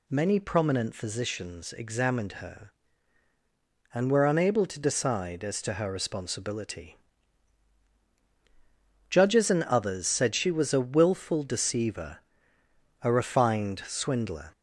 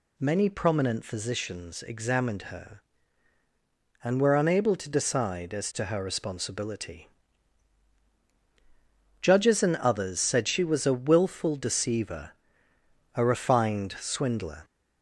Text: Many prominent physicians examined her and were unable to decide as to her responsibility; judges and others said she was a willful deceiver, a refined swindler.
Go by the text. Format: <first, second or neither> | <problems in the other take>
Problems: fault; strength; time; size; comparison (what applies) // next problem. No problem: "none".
neither | none